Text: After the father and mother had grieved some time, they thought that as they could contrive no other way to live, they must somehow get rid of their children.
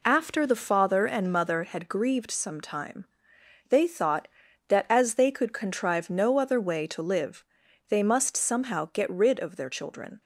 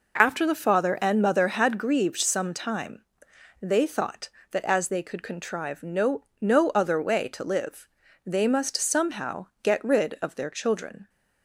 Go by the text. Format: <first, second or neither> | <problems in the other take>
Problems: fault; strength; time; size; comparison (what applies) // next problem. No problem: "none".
first | says "no" twice; at 6.4 s // pauses between "somehow" and "get"; slight; at 9.4 s; 0.16 s long